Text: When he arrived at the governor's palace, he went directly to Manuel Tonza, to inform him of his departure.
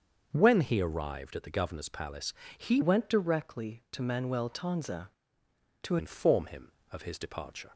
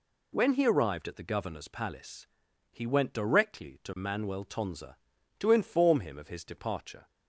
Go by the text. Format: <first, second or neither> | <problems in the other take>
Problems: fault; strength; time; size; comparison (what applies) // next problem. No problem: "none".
second | starts louder than the rest; until 1.3 s; 6.5 dB // changes voice from "went" to "to"; from 2.8 to 5.9 s; 3.1 s long